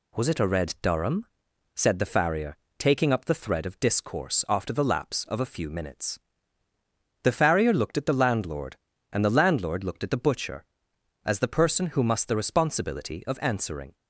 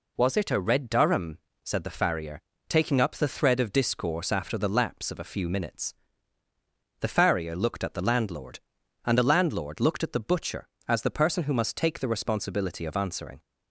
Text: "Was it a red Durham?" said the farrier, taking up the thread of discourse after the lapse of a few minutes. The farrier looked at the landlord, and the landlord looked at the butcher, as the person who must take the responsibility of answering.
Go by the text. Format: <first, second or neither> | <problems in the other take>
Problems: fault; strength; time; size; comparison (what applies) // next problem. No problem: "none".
second | skips "take"; at 12.2 s